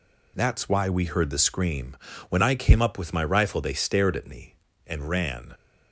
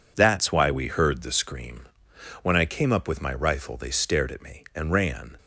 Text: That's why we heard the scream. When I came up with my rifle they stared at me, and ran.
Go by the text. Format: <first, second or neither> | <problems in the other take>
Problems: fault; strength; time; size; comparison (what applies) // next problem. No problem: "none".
neither | none